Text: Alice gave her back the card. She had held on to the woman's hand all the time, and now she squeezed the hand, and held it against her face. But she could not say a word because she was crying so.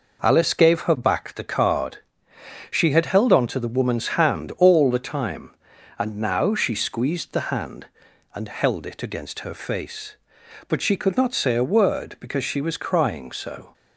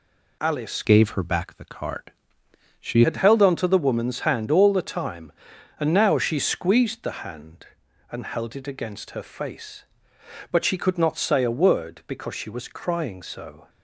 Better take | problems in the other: first | changes voice from "gave" to "She"; from 0.8 to 3.0 s; 2.2 s long

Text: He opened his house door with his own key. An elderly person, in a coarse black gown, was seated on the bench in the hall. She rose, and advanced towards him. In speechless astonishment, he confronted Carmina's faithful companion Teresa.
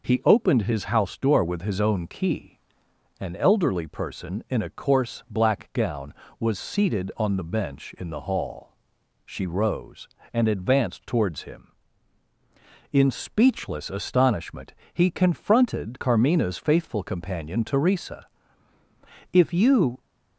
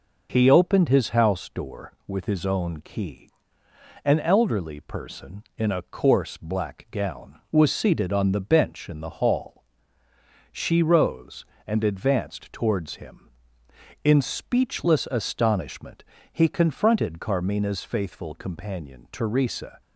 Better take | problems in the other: second | goes on to say "If you"; noticeable; from 19.3 s on; 0.68 s long

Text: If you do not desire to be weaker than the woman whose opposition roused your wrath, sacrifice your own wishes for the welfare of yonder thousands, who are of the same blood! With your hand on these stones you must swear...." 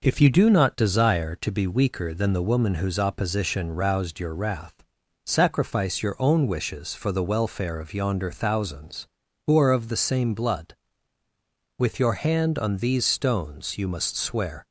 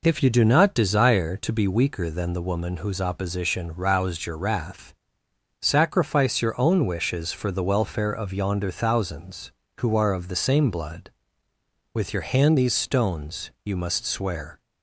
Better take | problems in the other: first | skips "on"; at 12.5 s

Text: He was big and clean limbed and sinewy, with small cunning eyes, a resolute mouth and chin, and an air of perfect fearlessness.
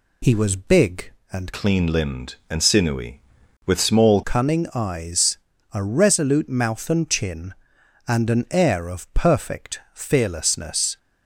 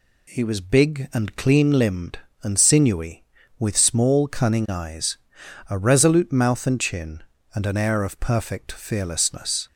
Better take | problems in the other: second | changes voice from "clean" to "small"; from 1.5 to 4.2 s; 2.7 s long

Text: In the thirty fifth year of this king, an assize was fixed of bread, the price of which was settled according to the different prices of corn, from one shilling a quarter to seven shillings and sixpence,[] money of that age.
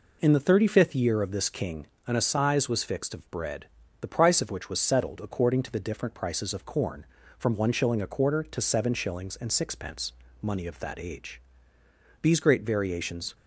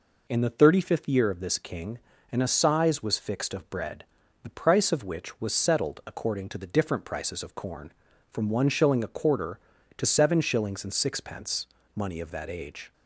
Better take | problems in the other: second | goes on to say "These great variations"; noticeable; from 12.2 s on; 1.1 s long

